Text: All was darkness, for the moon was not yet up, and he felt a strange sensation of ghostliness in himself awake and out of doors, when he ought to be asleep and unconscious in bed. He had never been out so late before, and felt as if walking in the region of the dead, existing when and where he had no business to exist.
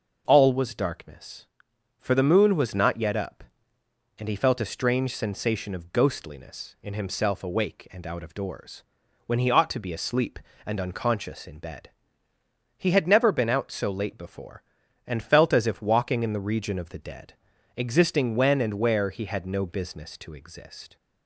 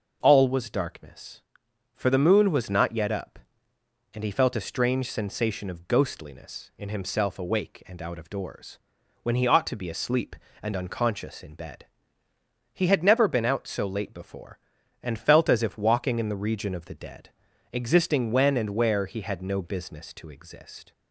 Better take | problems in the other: neither | none

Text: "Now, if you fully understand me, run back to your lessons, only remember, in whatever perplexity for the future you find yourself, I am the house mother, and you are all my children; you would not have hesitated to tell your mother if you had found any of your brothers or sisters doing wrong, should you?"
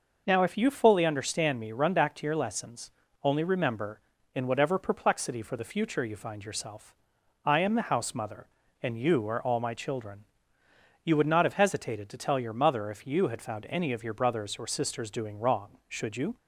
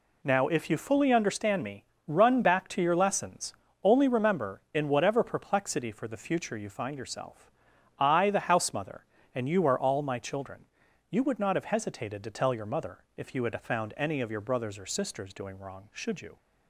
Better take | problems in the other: first | skips "am"; at 8.2 s

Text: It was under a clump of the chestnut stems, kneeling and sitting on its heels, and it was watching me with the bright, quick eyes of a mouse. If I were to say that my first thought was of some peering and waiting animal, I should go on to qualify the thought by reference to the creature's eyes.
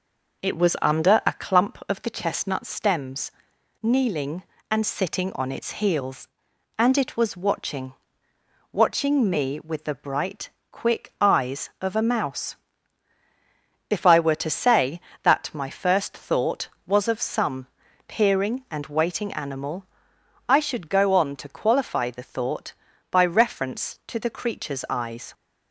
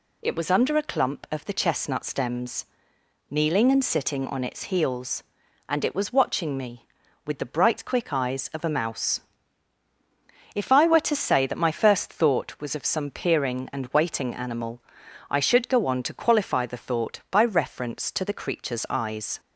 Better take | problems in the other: second | says "watching" twice; at 8.6 s // pauses between "some" and "peering"; at 17.6 s; 0.42 s long

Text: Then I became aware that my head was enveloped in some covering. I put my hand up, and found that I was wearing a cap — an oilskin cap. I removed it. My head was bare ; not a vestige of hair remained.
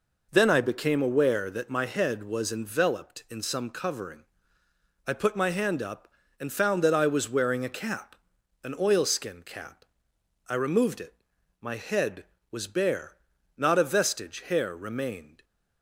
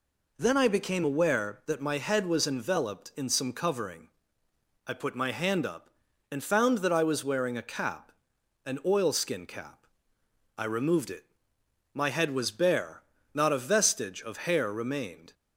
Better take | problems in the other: second | skips "of"; at 14.4 s

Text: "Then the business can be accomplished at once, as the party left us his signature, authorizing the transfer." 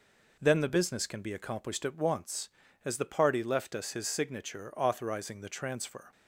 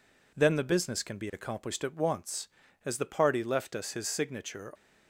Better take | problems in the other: first | stops before "authorizing the transfer"; at 4.7 s

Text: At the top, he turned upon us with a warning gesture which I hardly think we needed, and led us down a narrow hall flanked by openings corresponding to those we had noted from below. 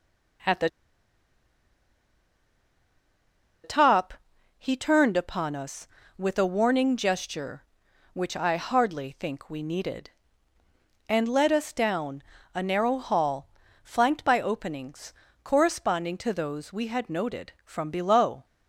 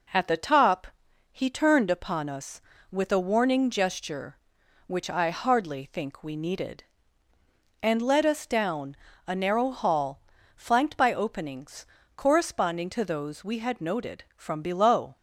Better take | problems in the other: second | pauses between "the" and "top"; strong; at 0.6 s; 2.9 s long // pauses between "down" and "a"; slight; at 12.2 s; 0.32 s long; slight in the second // pauses between "hall" and "flanked"; slight; at 13.4 s; 0.34 s long; slight in the second // pauses between "openings" and "corresponding"; slight; at 15.1 s; 0.30 s long; slight in the second

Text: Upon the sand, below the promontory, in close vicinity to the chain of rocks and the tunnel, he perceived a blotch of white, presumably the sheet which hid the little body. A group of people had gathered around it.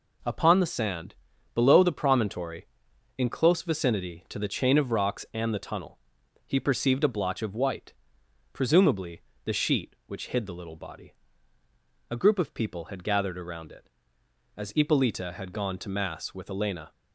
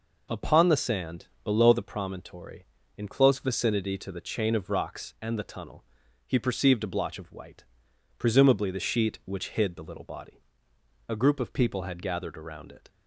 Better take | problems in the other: second | pauses between "presumably" and "the"; slight; at 9.2 s; 0.24 s long // goes on to say "As Ippolita had gone to mass with Elena"; strong; from 14.5 s on; 2.3 s long

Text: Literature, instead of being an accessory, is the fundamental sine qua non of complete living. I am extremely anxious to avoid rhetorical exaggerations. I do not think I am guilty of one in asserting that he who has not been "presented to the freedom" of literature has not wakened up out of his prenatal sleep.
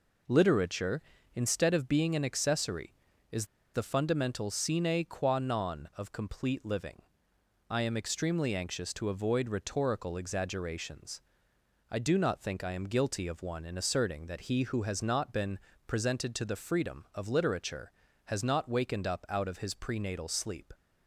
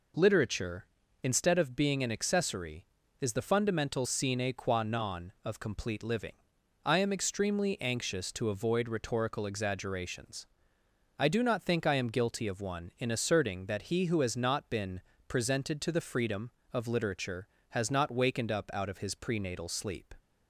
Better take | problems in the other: second | pauses between "is" and "the"; slight; at 3.4 s; 0.29 s long // pauses between "been" and "presented"; slight; at 15.5 s; 0.28 s long; slight in the second

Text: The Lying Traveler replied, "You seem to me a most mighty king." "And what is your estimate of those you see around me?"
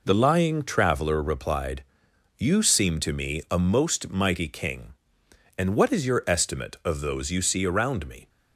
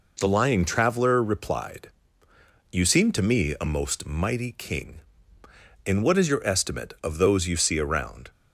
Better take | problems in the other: first | stops before "me"; at 8.2 s

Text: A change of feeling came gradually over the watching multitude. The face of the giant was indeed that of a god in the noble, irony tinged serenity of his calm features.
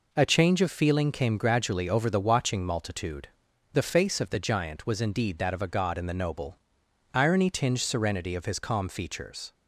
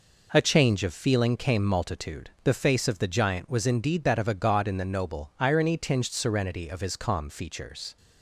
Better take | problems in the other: first | skips "gradually over the watching"; at 1.6 s

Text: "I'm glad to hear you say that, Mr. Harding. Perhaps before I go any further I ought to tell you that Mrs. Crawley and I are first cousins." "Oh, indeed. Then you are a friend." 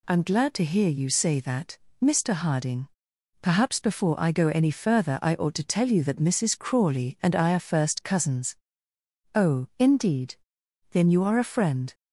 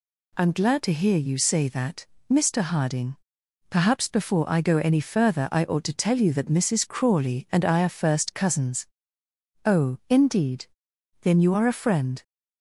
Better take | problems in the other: neither | none

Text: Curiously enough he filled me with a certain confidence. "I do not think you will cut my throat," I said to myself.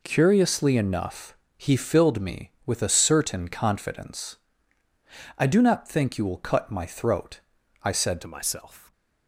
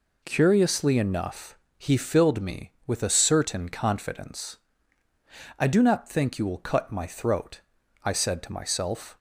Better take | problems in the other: second | pauses between "enough" and "he"; slight; at 1.3 s; 0.22 s long; slight in the second // changes voice at "to"; from 8.2 s on; 0.7 s long

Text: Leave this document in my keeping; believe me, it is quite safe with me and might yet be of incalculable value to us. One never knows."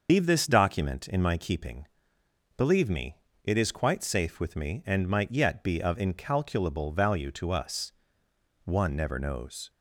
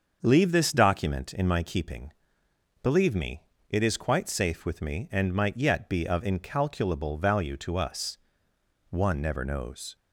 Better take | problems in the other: second | loses the start of "Leave"; at 0.0 s; 130 ms // starts louder than the rest; until 1.1 s; 6 dB; also in the second

